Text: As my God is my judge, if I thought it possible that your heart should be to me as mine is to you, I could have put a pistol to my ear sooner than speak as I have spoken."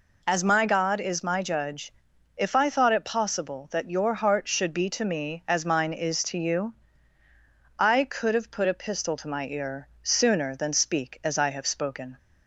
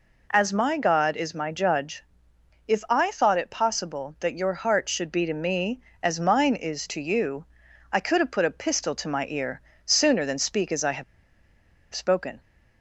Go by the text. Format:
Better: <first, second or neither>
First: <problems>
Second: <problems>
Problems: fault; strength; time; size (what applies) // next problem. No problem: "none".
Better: first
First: pauses between "ear" and "sooner"; slight; at 9.8 s; 0.16 s long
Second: pauses between "ear" and "sooner"; slight; at 9.6 s; 0.24 s long // pauses between "have" and "spoken"; noticeable; at 11.0 s; 0.89 s long